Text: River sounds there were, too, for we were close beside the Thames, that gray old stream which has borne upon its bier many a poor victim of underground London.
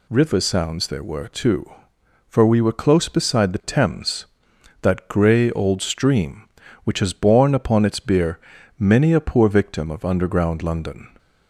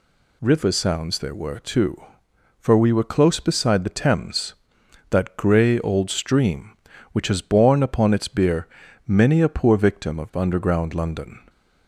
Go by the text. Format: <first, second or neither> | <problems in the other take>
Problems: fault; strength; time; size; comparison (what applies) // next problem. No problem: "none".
neither | pauses between "bier" and "many"; the same in both